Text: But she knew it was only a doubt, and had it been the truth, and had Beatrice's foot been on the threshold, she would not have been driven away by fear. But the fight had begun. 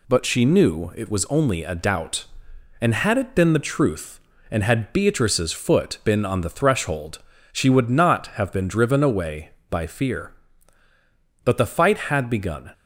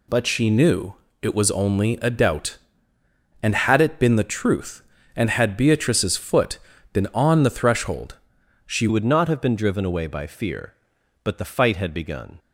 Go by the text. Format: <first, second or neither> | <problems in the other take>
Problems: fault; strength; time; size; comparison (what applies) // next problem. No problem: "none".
first | pauses between "knew" and "it"; slight; at 0.9 s; 0.26 s long // pauses between "foot" and "been"; slight; at 6.5 s; 0.34 s long // changes voice at "would"; from 8.8 s on; 3.5 s long